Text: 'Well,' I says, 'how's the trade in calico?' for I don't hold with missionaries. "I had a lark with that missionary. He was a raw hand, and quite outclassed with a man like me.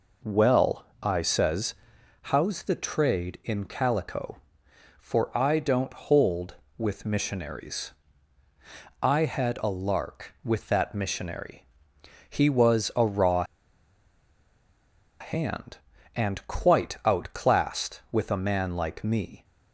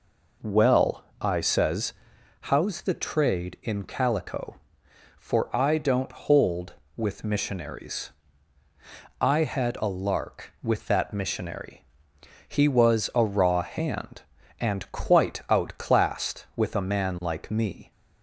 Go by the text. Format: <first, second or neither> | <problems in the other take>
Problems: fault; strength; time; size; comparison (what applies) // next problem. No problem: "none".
second | pauses between "raw" and "hand"; strong; at 13.4 s; 1.7 s long